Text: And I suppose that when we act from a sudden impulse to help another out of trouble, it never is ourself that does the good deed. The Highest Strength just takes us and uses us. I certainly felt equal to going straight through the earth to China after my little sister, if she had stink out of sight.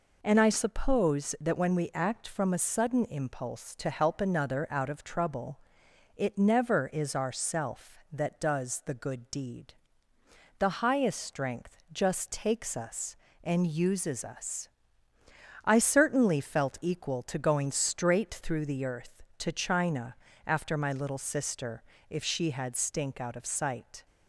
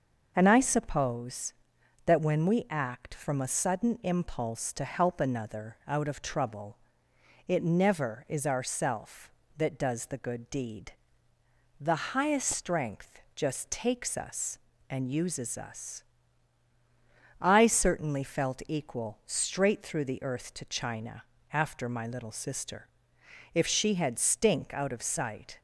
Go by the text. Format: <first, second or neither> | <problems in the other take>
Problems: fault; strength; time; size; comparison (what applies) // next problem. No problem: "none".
first | skips "to going"; at 19.2 s // pauses between "China" and "after"; slight; at 21.2 s; 0.30 s long; slight in the first